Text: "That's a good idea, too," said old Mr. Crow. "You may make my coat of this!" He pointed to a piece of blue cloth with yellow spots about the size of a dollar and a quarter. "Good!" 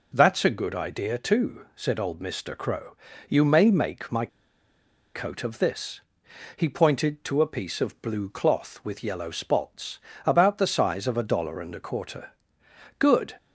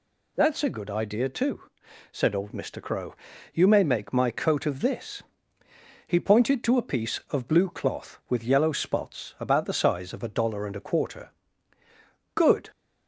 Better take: second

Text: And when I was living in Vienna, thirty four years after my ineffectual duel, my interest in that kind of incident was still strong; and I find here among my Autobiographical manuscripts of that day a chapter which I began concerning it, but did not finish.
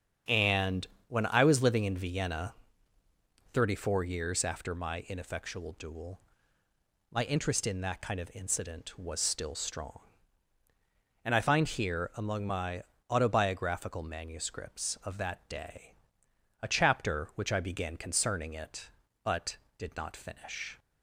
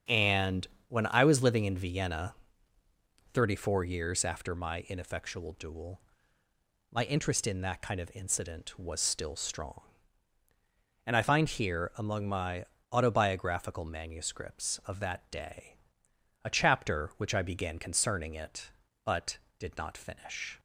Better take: neither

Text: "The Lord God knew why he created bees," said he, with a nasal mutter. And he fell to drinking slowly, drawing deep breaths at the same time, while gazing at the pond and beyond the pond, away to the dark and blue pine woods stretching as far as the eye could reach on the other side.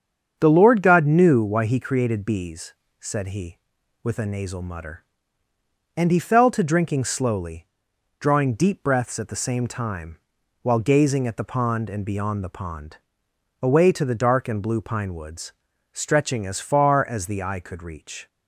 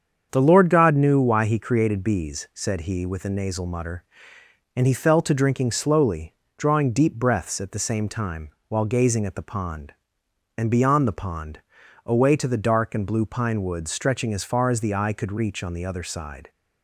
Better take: second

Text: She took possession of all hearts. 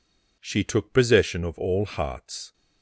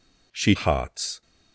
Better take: first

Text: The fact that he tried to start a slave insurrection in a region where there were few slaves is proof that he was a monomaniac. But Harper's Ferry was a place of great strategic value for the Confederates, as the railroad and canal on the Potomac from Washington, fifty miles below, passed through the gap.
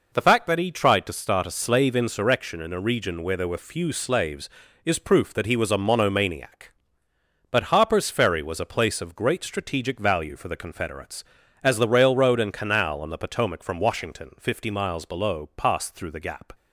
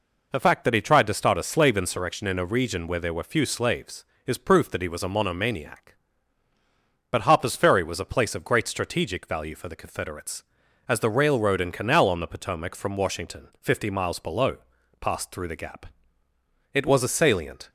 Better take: first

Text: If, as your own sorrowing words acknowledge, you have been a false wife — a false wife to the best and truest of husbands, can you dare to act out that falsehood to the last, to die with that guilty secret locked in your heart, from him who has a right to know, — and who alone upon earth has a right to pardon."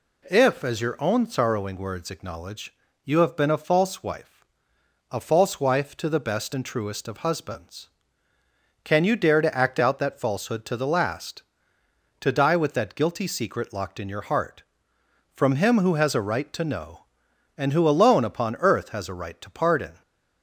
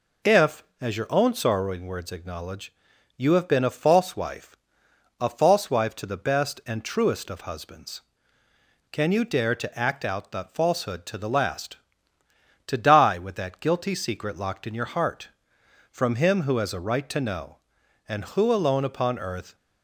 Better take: first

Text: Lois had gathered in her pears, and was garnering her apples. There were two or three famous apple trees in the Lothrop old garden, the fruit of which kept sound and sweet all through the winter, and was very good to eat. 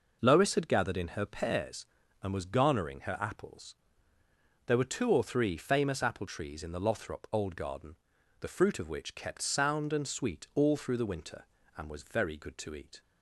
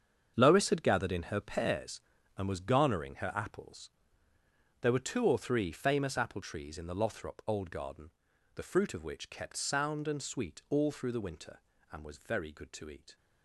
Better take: first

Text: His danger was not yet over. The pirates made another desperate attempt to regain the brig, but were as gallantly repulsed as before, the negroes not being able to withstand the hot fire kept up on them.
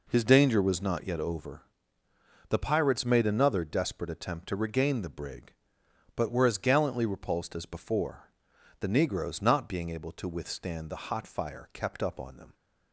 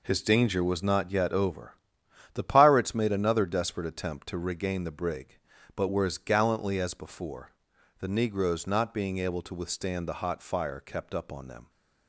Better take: first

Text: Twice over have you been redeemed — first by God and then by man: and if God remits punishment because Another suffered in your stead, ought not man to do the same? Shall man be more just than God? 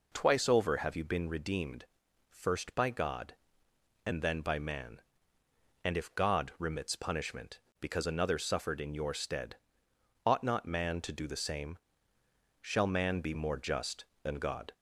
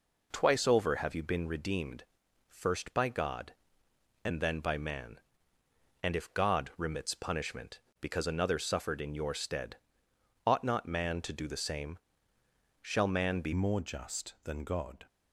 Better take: first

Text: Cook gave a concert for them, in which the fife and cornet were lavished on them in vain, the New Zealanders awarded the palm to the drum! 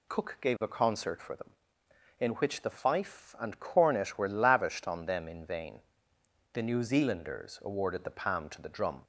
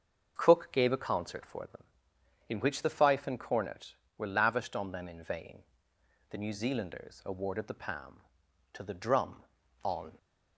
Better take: first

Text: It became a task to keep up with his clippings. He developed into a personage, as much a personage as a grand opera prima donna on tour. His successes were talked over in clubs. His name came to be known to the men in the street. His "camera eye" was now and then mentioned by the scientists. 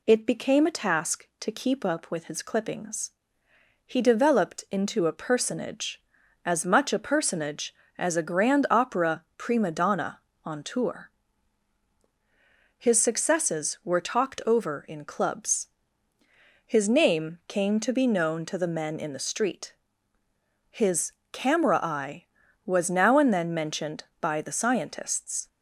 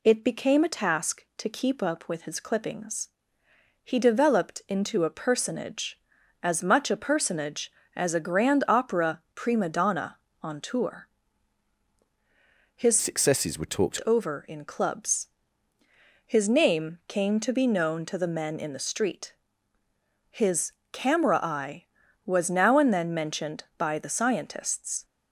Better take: first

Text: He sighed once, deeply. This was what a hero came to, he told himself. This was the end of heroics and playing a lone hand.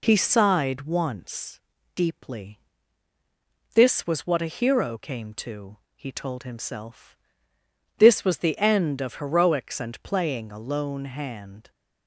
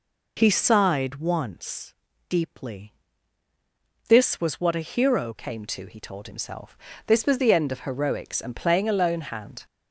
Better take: first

